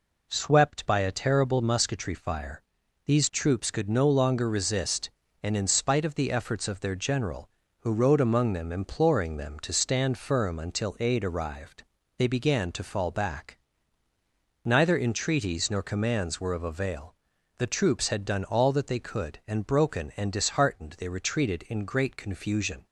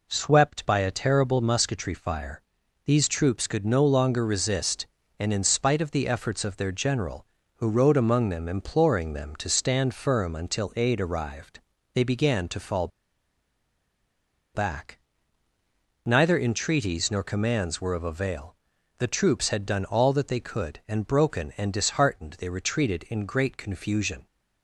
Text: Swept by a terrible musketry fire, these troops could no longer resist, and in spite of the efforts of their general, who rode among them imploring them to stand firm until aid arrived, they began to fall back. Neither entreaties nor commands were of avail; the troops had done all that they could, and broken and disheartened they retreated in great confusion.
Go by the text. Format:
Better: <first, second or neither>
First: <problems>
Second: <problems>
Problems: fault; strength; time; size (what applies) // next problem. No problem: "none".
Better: first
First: none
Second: pauses between "fall" and "back"; strong; at 12.8 s; 1.6 s long